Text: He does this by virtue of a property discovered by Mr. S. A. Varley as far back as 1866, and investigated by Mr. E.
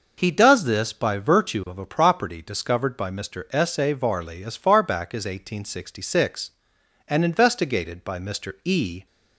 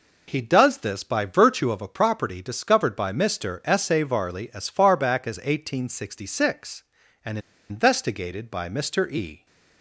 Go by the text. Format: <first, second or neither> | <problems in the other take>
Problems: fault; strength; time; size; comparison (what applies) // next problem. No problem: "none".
first | pauses between "and" and "investigated"; slight; at 7.3 s; 0.30 s long